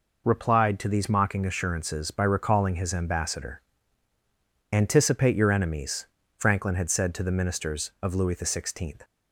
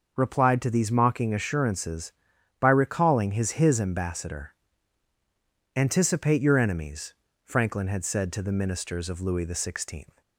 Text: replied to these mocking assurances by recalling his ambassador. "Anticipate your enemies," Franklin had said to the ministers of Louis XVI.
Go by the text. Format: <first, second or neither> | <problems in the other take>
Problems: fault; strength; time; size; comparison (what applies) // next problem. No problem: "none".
first | starts louder than the rest; noticeable; until 1.1 s; 6 dB // says "his" twice; at 3.5 s